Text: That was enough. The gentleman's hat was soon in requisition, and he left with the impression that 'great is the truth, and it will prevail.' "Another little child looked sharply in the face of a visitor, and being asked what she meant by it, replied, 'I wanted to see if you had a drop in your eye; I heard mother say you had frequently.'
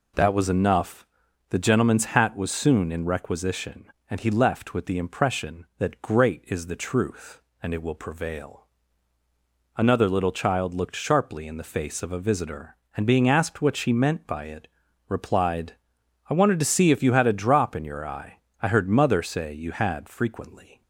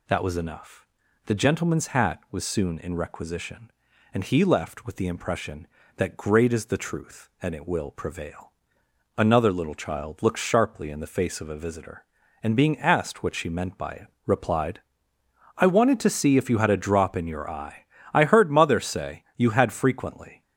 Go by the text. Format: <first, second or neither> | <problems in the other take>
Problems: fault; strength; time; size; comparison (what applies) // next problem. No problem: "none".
neither | none